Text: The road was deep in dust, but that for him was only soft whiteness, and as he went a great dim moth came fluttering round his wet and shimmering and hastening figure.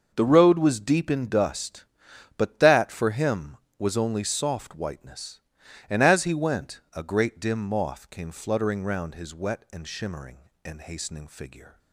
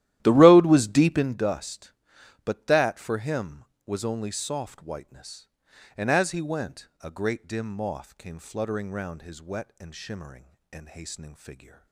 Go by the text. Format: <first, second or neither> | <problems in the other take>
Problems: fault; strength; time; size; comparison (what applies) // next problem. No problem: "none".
first | starts louder than the rest; strong; until 1.5 s; 13.5 dB